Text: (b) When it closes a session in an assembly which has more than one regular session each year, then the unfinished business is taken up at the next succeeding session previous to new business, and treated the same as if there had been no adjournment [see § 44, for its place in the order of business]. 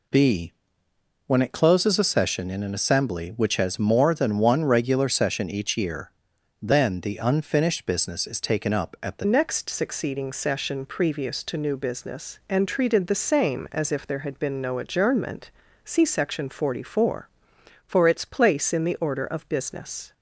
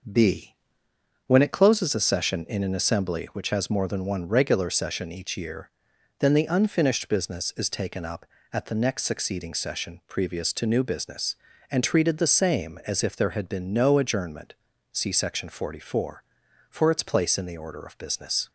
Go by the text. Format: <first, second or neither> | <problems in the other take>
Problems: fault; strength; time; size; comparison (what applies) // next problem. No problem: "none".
second | changes voice at "next"; from 9.2 s on; 10.9 s long // pauses between "adjournment" and "see"; slight; at 15.4 s; 0.36 s long; also in the second